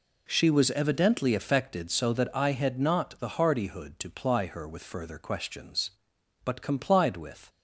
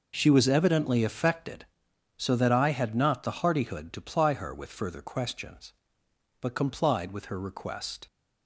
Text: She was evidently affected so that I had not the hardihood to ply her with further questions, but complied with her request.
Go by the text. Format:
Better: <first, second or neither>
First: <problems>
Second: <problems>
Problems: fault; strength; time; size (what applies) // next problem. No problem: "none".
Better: second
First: stops before "her request"; at 7.4 s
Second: none